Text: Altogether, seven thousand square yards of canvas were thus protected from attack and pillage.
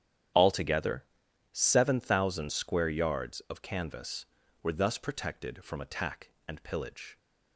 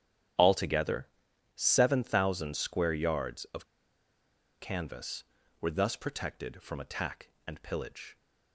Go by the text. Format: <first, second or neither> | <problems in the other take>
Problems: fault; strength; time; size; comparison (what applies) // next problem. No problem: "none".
first | starts louder than the rest; strong; until 1.8 s; 10 dB; strong in the first // pauses between "of" and "canvas"; noticeable; at 3.6 s; 0.94 s long